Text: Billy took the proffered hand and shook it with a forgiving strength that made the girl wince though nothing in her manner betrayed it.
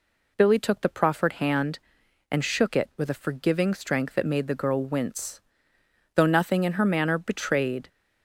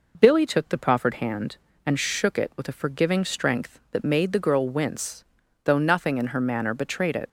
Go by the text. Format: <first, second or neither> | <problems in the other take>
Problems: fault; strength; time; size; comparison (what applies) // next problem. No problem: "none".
second | pauses between "wince" and "though"; noticeable; at 5.3 s; 0.74 s long; also in the second // stops before "it"; at 7.8 s